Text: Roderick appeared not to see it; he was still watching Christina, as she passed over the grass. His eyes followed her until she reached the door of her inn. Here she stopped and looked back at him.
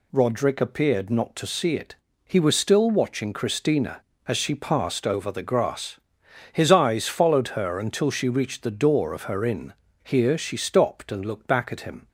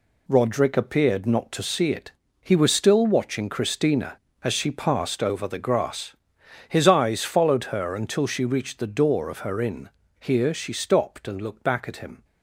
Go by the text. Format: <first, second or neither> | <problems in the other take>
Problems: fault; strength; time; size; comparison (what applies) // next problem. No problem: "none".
first | gets quieter; strong; throughout; 7.5 dB